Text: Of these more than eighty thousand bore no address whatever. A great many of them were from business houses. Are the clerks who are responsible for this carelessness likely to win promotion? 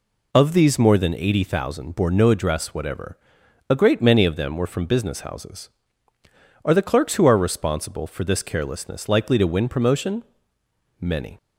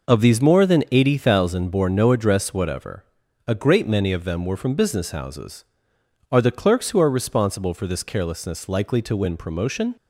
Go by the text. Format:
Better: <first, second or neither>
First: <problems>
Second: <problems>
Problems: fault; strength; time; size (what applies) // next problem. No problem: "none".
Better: second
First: goes on to say "Many"; slight; from 10.9 s on; 0.36 s long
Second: none